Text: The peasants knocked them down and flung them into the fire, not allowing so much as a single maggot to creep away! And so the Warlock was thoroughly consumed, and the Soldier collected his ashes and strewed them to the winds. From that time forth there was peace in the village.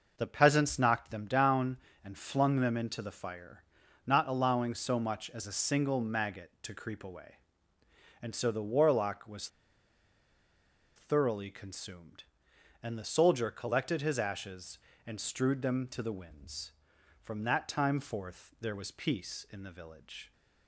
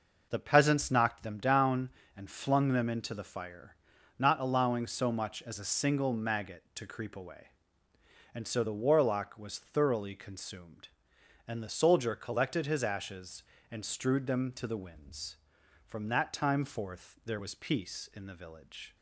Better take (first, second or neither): second